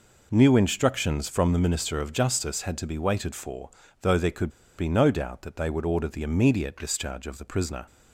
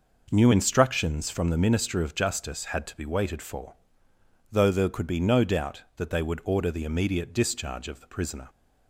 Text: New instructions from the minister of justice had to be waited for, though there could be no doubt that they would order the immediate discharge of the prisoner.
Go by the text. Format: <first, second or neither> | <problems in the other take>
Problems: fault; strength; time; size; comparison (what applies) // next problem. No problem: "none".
second | pauses between "could" and "be"; slight; at 4.4 s; 0.29 s long